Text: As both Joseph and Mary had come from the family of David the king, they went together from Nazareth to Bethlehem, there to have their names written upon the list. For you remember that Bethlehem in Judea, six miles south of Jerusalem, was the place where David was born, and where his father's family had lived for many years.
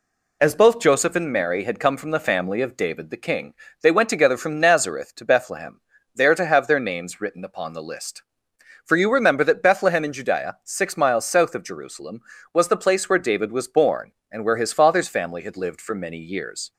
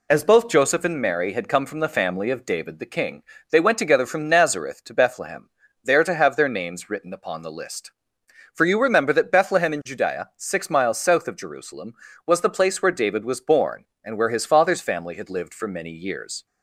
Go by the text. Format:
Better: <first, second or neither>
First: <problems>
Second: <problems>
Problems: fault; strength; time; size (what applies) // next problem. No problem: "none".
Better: neither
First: none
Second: none